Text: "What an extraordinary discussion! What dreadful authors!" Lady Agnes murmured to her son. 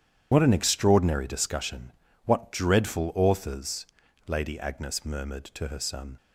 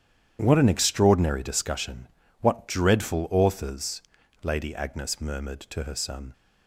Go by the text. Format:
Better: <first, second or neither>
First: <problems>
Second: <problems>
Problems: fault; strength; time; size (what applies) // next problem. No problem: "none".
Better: second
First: loses the start of "What"; at 0.3 s; 80 ms // starts louder than the rest; strong; until 1.3 s; 9.5 dB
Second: starts louder than the rest; strong; until 1.4 s; 9.5 dB